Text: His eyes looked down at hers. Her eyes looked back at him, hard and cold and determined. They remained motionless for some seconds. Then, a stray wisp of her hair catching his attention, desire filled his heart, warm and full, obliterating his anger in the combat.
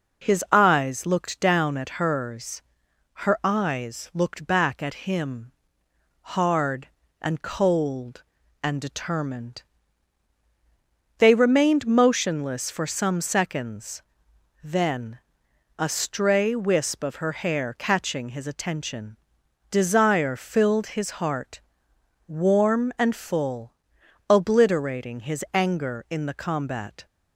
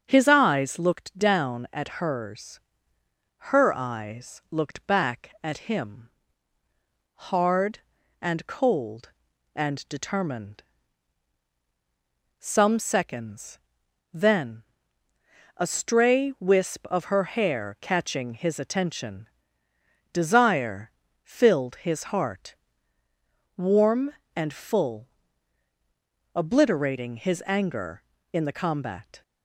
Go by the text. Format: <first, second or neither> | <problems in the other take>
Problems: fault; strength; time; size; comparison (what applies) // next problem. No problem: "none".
first | starts louder than the rest; until 1.0 s; 7 dB // skips "They remained motionless for"; at 11.5 s // pauses between "desire" and "filled"; slight; at 20.9 s; 0.32 s long